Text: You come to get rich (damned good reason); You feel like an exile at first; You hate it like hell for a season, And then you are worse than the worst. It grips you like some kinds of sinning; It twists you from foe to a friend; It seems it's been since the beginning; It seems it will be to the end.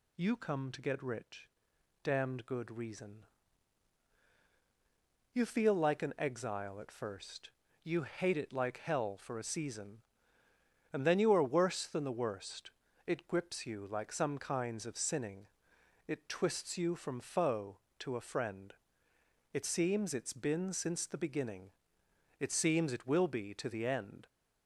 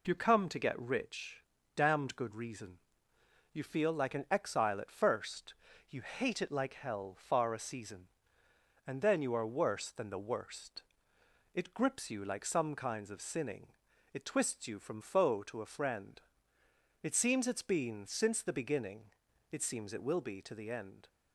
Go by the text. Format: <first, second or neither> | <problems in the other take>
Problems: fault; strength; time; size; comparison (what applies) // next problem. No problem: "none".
first | says "far" for "for"; at 7.1 s